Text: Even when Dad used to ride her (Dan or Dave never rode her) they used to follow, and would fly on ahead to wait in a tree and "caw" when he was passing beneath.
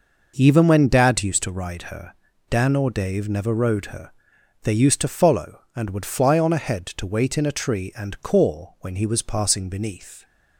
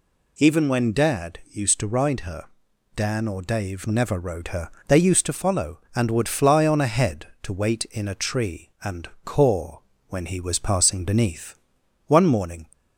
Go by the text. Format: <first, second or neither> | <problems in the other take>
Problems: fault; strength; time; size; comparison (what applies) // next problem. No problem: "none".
first | pauses between "and" and "caw"; slight; at 9.0 s; 0.16 s long // pauses between "caw" and "when"; slight; at 9.7 s; 0.30 s long // goes on to say "One morning"; from 12.0 s on; 0.58 s long